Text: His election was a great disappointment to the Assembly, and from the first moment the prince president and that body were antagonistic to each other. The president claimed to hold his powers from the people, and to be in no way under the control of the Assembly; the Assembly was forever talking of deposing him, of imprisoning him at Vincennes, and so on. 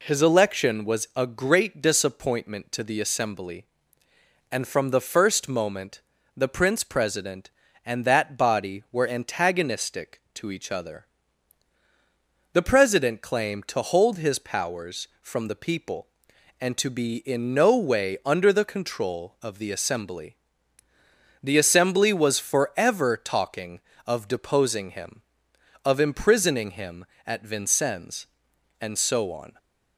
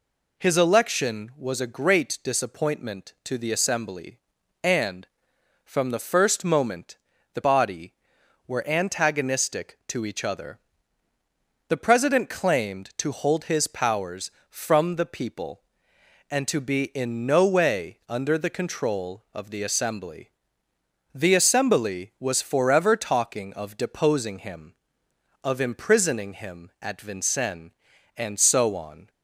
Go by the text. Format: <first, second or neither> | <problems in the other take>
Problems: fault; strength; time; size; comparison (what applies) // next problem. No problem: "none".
first | pauses between "moment" and "the"; slight; at 6.9 s; 0.36 s long; slight in the first // skips "prince president and that"; at 7.4 s